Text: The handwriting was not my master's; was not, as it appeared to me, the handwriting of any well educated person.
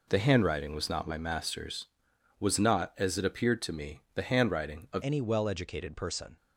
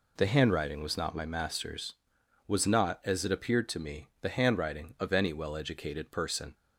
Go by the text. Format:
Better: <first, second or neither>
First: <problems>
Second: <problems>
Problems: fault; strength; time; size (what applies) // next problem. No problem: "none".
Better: second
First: changes voice at "any"; from 5.0 s on; 1.3 s long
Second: none